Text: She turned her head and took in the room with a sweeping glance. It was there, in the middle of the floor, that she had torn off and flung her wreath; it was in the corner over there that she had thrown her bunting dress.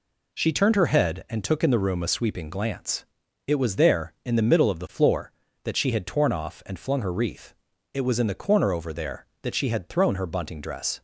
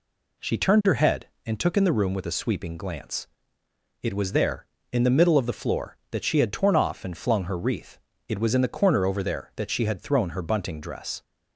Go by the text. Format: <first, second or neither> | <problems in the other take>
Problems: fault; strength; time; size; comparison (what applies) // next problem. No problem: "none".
second | skips "with"; at 2.0 s